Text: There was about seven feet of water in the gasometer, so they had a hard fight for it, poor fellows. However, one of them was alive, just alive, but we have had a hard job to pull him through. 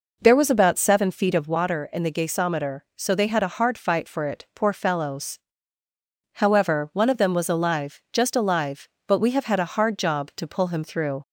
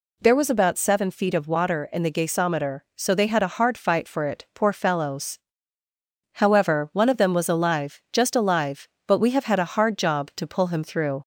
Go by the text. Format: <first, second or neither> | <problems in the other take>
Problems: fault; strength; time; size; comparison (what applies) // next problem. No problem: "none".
second | starts louder than the rest; noticeable; until 1.6 s; 4.5 dB